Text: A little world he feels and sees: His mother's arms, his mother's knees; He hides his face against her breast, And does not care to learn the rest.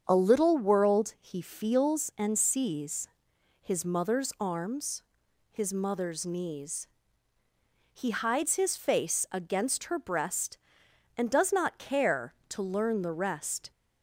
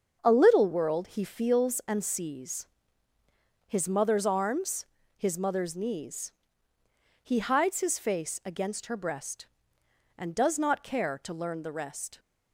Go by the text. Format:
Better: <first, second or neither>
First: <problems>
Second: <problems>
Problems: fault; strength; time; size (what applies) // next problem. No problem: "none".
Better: neither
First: starts louder than the rest; until 1.0 s; 7 dB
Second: starts louder than the rest; until 1.2 s; 6.5 dB